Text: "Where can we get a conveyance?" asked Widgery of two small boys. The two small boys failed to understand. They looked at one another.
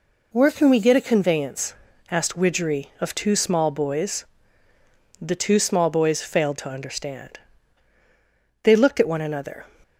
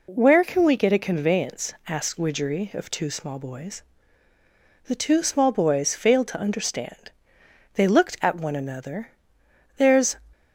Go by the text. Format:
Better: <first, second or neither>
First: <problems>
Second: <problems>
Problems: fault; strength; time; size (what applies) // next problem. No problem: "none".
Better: first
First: none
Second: goes on to say "There's"; slight; from 9.7 s on; 0.38 s long